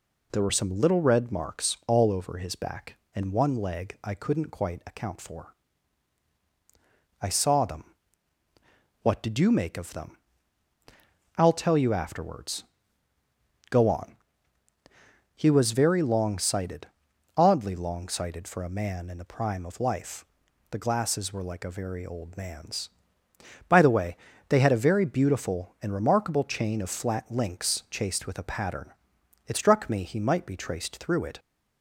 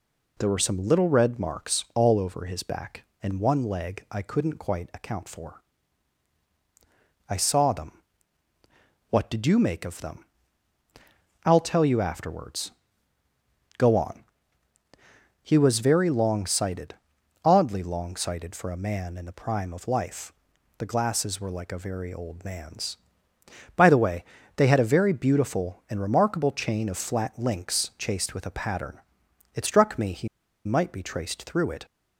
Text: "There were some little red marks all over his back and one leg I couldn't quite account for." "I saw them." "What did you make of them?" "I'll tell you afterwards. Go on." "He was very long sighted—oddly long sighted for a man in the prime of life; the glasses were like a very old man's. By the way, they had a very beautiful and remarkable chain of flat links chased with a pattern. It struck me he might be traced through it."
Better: first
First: none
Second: pauses between "he" and "might"; at 30.2 s; 0.37 s long

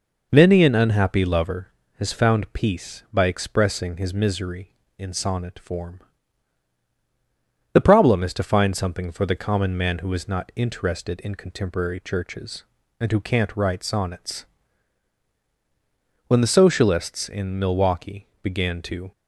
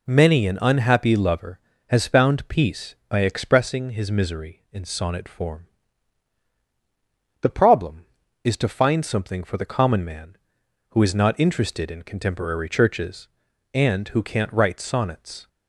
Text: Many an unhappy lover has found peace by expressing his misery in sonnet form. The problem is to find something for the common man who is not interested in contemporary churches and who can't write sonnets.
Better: second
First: goes on to say "When the socialists in Milwaukee began to"; strong; from 16.2 s on; 2.8 s long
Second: none

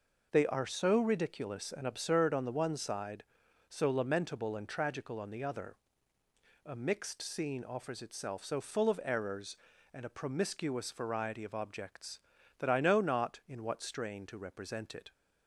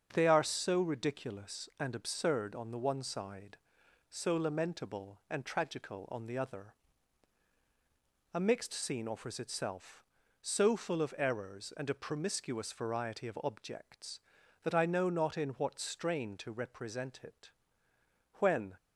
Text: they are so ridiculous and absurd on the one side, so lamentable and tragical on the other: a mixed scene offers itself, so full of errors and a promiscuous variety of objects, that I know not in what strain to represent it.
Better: first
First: none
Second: starts louder than the rest; strong; until 1.1 s; 7.5 dB // goes on to say "When"; slight; from 18.3 s on; 0.36 s long

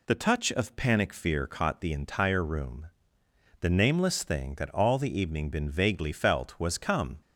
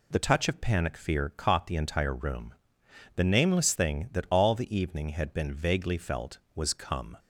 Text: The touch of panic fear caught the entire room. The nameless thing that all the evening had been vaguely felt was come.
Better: second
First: skips "had"; at 5.4 s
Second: none

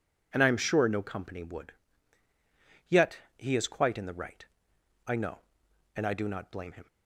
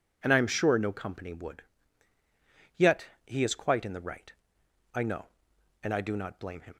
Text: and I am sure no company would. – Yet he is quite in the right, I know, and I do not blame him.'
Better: neither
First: pauses between "Yet" and "he"; slight; at 3.1 s; 0.20 s long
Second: pauses between "Yet" and "he"; slight; at 3.0 s; 0.20 s long

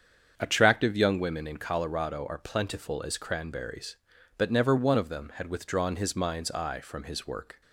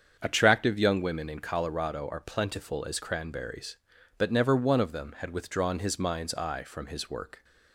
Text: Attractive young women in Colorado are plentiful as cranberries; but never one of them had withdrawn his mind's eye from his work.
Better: neither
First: starts louder than the rest; strong; until 1.3 s; 7.5 dB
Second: starts louder than the rest; strong; until 1.2 s; 7.5 dB

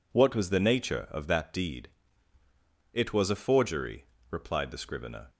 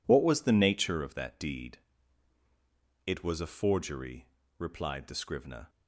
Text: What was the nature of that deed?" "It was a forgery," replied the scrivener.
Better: neither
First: none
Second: none

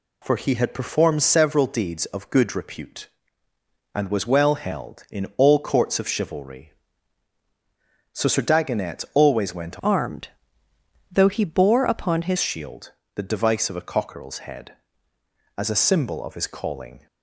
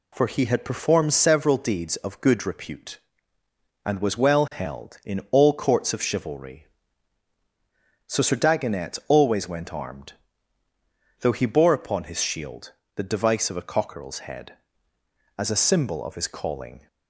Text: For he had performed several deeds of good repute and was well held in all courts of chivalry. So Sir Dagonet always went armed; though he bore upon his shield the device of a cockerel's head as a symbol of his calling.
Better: second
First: changes voice from "armed" to "his"; from 9.8 to 12.3 s; 2.5 s long // pauses between "shield" and "the"; slight; at 12.9 s; 0.22 s long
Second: pauses between "shield" and "the"; slight; at 12.7 s; 0.22 s long

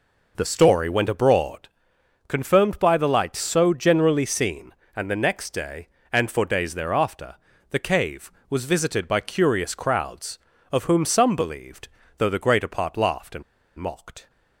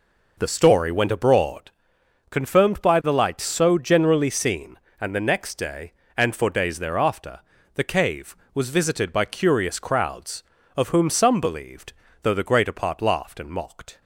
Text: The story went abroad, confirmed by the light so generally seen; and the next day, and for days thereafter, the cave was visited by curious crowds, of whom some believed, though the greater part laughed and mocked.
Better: second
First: pauses between "and" and "mocked"; slight; at 13.4 s; 0.36 s long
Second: none

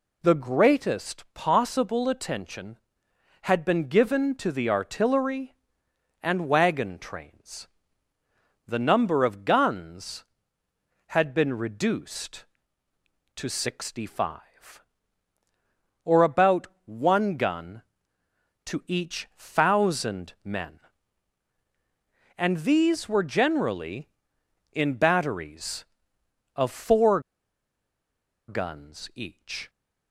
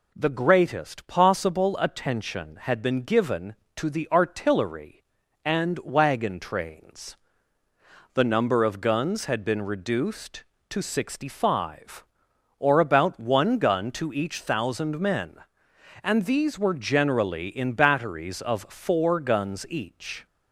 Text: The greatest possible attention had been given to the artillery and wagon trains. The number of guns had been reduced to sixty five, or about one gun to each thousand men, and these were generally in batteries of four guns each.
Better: second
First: pauses between "about" and "one"; slight; at 16.6 s; 0.18 s long // pauses between "four" and "guns"; strong; at 27.1 s; 1.2 s long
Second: none

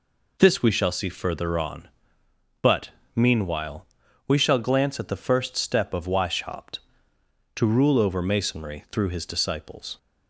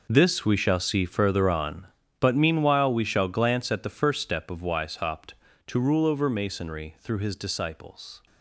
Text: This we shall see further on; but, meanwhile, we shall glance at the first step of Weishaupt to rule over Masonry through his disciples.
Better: first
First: none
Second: gets quieter; strong; throughout; 14 dB

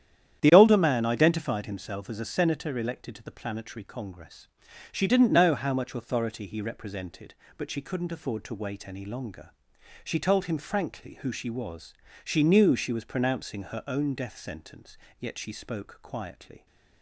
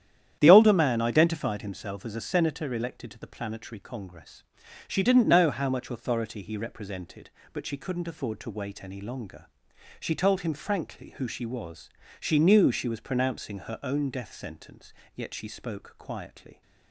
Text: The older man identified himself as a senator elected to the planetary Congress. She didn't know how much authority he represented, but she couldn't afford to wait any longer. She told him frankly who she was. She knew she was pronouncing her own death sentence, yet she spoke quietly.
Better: neither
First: starts louder than the rest; strong; until 1.4 s; 9.5 dB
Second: starts louder than the rest; strong; until 1.4 s; 10 dB

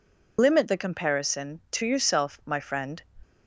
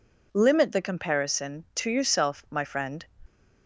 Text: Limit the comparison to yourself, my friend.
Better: second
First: loses the start of "Limit"; at 0.3 s; 95 ms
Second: none

